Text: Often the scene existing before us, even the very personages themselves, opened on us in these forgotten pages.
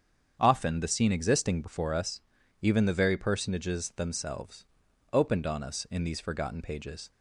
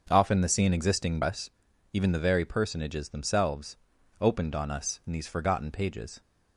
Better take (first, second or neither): first